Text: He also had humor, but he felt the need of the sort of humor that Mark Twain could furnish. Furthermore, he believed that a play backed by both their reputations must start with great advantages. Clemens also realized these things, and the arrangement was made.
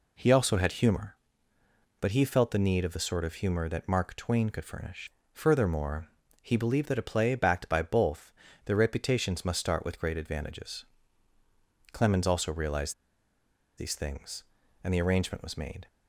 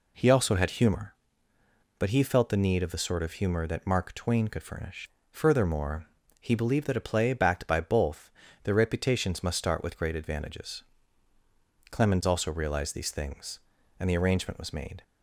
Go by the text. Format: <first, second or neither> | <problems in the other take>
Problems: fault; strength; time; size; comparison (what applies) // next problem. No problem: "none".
second | pauses between "both" and "their"; slight; at 8.3 s; 0.34 s long; slight in the second // pauses between "realized" and "these"; noticeable; at 12.9 s; 0.85 s long